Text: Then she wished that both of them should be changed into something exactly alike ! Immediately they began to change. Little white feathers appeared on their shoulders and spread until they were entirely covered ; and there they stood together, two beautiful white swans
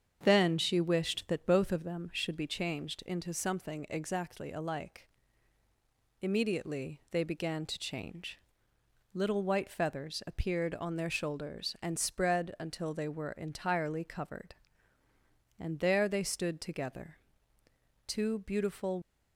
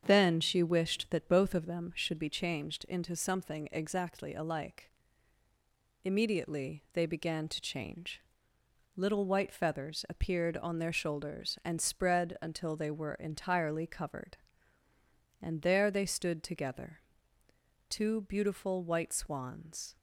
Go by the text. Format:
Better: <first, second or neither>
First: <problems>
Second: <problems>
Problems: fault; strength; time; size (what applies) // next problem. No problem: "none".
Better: second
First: starts louder than the rest; strong; until 1.2 s; 7.5 dB // stops before "white swans"; at 19.0 s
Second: starts louder than the rest; strong; until 1.0 s; 7.5 dB